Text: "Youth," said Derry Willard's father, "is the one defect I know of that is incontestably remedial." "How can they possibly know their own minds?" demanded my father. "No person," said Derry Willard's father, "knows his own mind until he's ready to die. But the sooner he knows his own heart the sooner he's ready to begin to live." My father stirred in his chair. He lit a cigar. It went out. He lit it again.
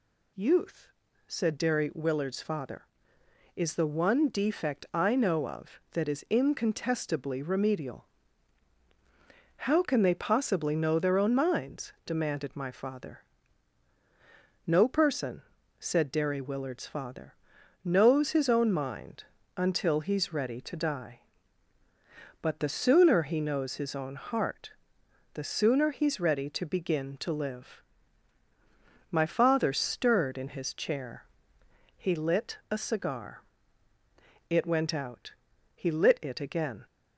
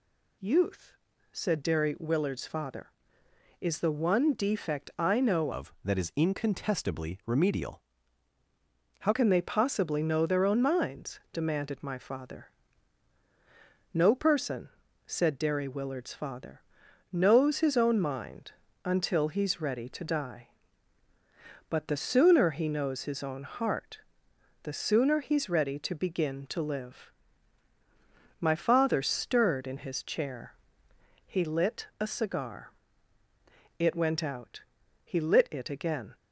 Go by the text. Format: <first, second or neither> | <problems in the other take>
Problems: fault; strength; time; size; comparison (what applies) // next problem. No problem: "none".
first | changes voice from "of" to "How"; from 5.5 to 9.1 s; 3.6 s long // pauses between "mind" and "until"; slight; at 18.5 s; 0.32 s long; slight in the first // pauses between "heart" and "the"; noticeable; at 23.9 s; 0.64 s long; noticeable in the first